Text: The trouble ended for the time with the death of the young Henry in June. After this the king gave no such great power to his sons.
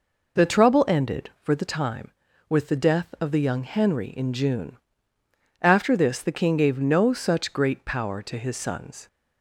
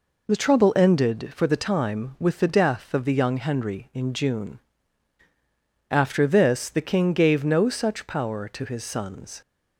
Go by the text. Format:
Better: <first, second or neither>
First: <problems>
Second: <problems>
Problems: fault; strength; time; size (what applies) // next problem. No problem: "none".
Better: first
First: none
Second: skips "great"; at 8.0 s